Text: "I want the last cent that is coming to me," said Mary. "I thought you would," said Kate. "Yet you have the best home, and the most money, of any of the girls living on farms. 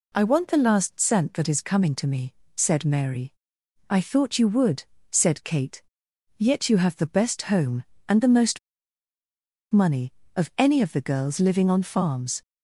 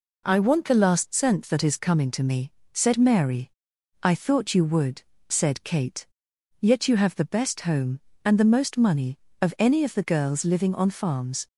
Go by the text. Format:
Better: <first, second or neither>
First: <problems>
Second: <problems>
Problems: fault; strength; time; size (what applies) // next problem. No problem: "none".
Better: second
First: pauses between "most" and "money"; at 8.5 s; 1.1 s long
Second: none